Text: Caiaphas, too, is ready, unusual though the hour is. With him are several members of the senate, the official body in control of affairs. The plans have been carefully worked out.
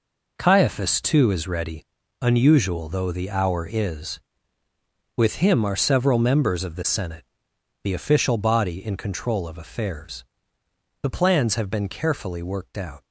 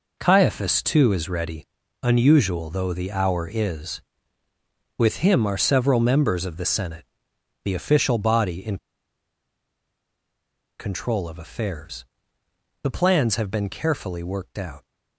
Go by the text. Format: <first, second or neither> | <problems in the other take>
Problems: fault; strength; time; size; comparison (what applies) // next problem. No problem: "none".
first | pauses between "in" and "control"; strong; at 8.7 s; 2.0 s long